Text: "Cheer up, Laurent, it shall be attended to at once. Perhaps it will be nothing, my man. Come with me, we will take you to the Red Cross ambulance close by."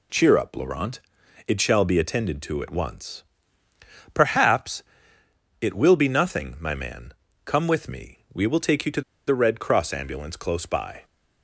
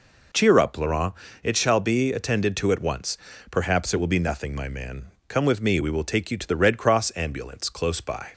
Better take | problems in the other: second | pauses between "Perhaps" and "it"; noticeable; at 4.8 s; 0.78 s long // pauses between "to" and "the"; slight; at 9.0 s; 0.26 s long

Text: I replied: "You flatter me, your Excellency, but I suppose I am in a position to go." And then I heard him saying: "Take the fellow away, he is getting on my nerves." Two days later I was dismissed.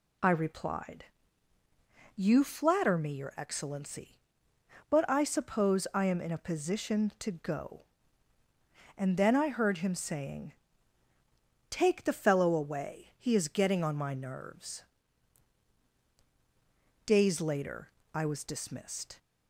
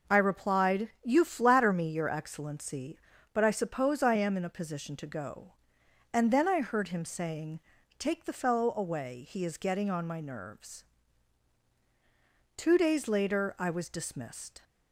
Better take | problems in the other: second | skips "Two"; at 15.9 s // pauses between "later" and "I"; slight; at 17.8 s; 0.24 s long

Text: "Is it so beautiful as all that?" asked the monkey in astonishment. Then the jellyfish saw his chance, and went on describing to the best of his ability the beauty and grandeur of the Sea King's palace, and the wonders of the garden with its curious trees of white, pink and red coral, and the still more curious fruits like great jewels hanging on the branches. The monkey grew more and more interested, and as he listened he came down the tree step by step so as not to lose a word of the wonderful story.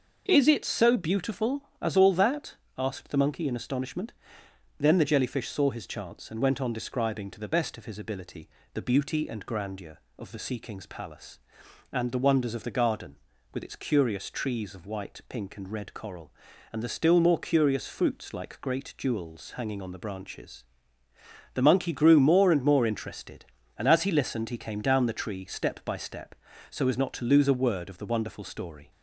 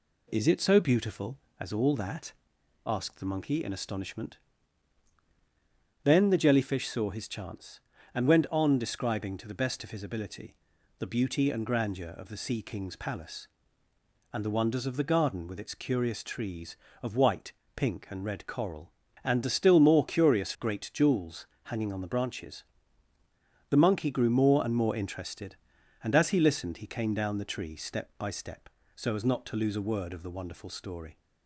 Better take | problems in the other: first | pauses between "ability" and "the"; at 10.5 s; 0.44 s long; slight in the first // skips "fruits like"; at 20.5 s // pauses between "jewels" and "hanging"; slight; at 21.4 s; 0.18 s long

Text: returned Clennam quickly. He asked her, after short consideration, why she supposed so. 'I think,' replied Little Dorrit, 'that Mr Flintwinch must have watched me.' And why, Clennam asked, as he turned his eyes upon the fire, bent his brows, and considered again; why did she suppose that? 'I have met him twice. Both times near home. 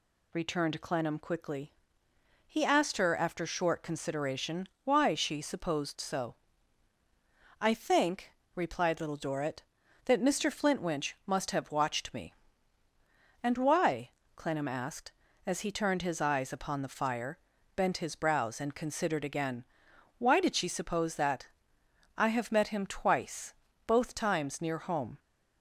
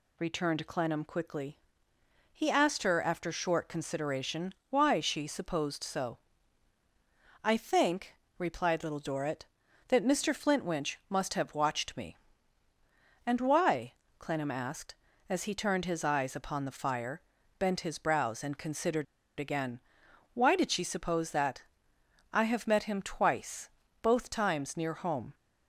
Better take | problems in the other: first | pauses between "considered" and "again"; slight; at 19.0 s; 0.33 s long

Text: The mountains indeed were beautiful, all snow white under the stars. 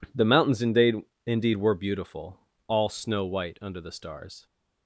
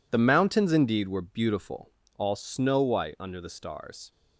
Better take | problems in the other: second | says "indeed" twice; at 1.2 s

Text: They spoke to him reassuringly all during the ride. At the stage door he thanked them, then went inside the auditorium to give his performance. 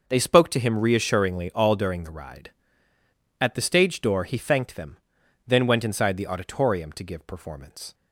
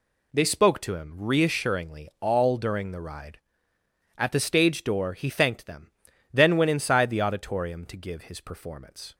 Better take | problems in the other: second | skips "his"; at 7.2 s

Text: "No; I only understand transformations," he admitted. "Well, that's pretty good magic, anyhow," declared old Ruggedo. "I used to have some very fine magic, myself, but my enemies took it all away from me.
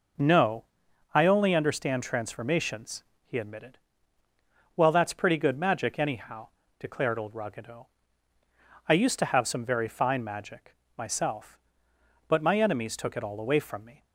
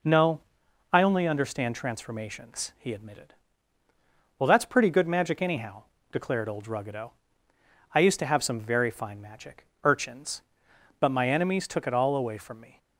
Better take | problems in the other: first | says "urchins" for "myself"; at 9.8 s

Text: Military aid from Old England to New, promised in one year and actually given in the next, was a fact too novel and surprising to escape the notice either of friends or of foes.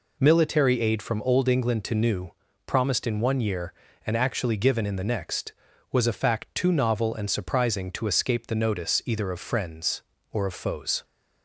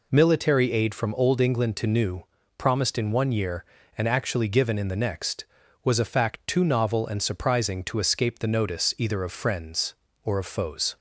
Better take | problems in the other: neither | none

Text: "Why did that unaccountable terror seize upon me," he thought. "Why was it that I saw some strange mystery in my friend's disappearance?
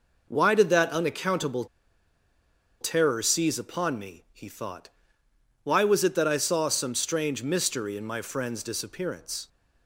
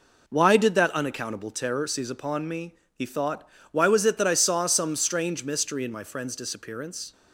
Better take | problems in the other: second | pauses between "unaccountable" and "terror"; at 1.6 s; 1.1 s long

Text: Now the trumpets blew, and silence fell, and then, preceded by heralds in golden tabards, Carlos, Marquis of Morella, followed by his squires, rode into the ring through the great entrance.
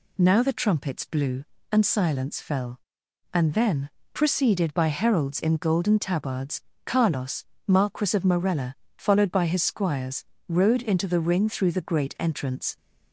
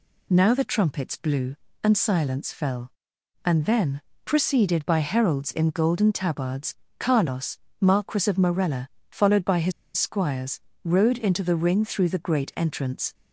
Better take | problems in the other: first | pauses between "his" and "squires"; slight; at 9.7 s; 0.25 s long

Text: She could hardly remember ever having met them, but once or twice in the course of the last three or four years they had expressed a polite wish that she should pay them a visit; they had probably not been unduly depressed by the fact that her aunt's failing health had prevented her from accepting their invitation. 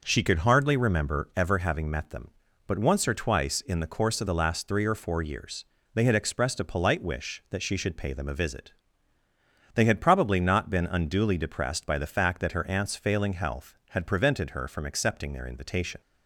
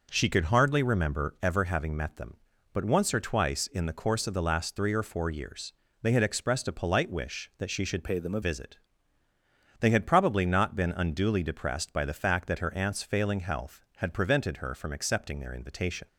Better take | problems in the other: first | pauses between "years" and "they"; slight; at 5.7 s; 0.30 s long; slight in the first // changes voice from "pay" to "a"; from 8.0 to 8.4 s; 0.4 s long

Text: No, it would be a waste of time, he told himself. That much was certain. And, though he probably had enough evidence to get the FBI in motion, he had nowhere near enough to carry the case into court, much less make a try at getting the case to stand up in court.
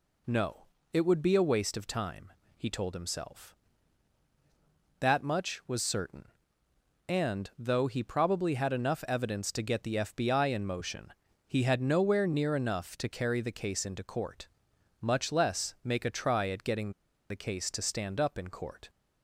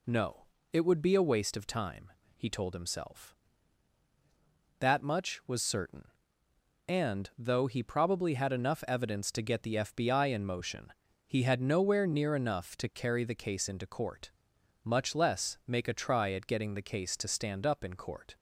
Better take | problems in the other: second | pauses between "getting" and "the"; at 16.9 s; 0.37 s long

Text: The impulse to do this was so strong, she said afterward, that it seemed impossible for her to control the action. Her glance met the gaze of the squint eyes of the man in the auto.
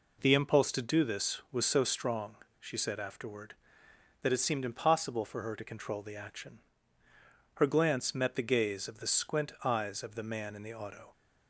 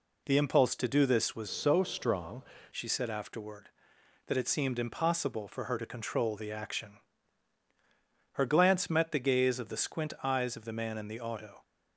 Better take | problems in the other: first | changes voice from "so" to "strong"; from 1.4 to 2.4 s; 1.0 s long

